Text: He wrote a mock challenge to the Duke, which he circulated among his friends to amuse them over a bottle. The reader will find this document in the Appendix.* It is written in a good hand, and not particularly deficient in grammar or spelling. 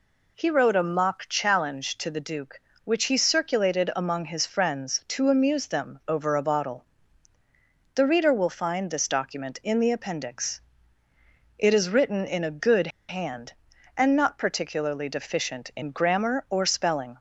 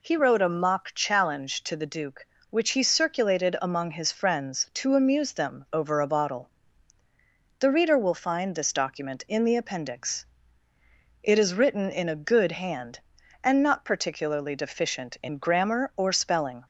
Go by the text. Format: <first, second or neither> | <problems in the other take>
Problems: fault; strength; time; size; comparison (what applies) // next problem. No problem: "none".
second | pauses between "good" and "hand"; slight; at 12.8 s; 0.20 s long